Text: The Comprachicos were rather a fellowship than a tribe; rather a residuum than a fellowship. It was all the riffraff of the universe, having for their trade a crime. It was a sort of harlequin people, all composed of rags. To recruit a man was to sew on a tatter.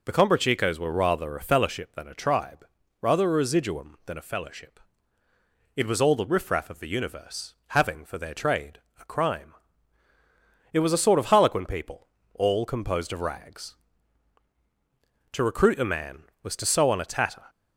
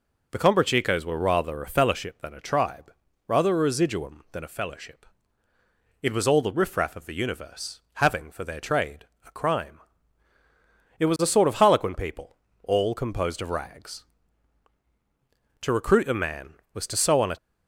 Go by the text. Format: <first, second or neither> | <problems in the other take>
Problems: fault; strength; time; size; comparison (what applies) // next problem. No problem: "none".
first | pauses between "trade" and "a"; slight; at 9.0 s; 0.20 s long; slight in the first // stops before "tatter"; at 17.3 s